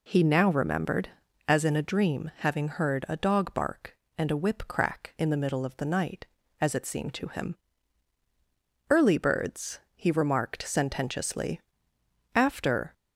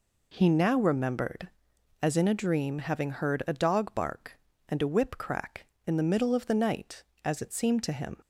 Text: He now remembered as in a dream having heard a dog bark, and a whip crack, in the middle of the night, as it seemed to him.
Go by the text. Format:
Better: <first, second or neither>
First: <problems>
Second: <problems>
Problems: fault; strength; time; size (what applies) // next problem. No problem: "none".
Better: second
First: goes on to say "Early birds he remarked sententiously after"; strong; from 8.8 s on; 4.0 s long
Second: none